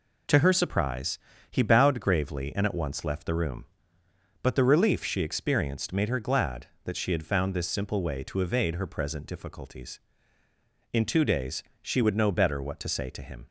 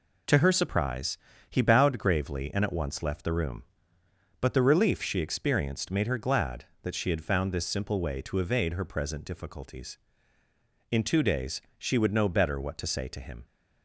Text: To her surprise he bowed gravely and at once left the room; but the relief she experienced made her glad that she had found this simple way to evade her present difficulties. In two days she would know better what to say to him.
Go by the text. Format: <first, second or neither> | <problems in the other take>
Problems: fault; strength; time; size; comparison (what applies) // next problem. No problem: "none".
neither | pauses between "surprise" and "he"; slight; the same in both // pauses between "days" and "she"; slight; the same in both